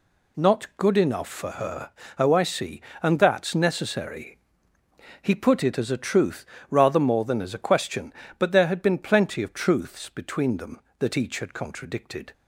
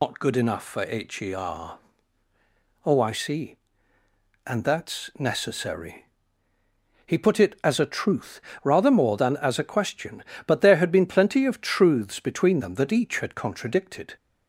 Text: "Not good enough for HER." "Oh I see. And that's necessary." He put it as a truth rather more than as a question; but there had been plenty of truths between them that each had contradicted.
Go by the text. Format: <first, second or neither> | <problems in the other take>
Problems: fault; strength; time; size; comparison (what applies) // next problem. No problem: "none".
first | loses the start of "Not"; at 0.0 s; 110 ms // pauses between "truth" and "rather"; slight; at 8.3 s; 0.24 s long; slight in the first